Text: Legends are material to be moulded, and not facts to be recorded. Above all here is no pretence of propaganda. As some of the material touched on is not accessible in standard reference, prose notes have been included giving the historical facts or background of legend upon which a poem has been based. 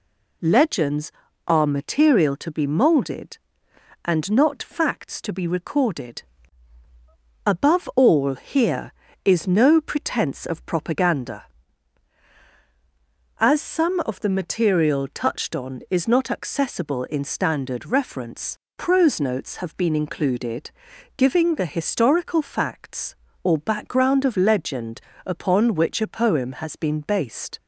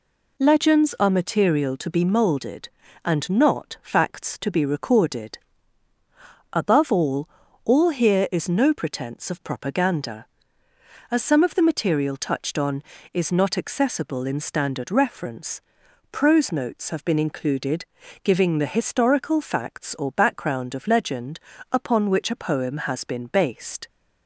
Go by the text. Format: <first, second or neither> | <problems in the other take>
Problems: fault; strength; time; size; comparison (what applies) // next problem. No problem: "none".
first | says "all" twice; at 7.6 s // pauses between "included" and "giving"; at 17.8 s; 0.40 s long; noticeable in the first // pauses between "legend" and "upon"; slight; at 21.3 s; 0.34 s long; slight in the first